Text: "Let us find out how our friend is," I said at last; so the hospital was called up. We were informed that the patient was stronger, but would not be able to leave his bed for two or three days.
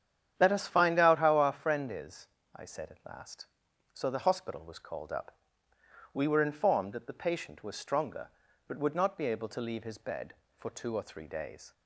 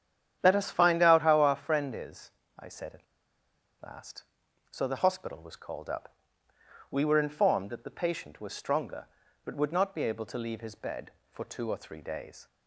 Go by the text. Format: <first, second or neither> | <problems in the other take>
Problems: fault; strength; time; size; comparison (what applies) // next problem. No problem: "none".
first | starts louder than the rest; strong; until 1.4 s; 9.5 dB; strong in the first // pauses between "at" and "last"; noticeable; at 3.0 s; 0.79 s long